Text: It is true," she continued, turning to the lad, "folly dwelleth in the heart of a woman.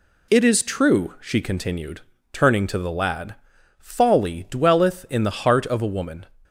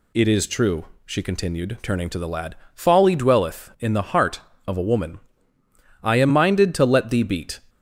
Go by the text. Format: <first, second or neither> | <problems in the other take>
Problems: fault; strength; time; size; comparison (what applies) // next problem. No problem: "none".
first | goes on to say "I am minded to let thee beat"; from 6.0 s on; 1.5 s long